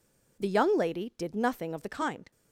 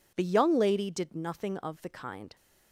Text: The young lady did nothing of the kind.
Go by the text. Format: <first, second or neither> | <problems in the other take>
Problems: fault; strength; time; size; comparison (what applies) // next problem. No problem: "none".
neither | none